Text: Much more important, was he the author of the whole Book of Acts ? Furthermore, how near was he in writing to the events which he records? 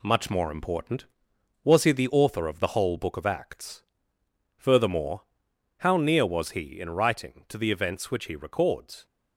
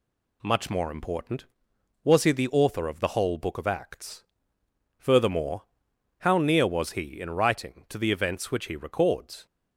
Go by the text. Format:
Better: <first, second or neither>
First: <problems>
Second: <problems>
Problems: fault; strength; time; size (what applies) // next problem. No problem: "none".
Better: second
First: gets quieter; noticeable; throughout; 5 dB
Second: none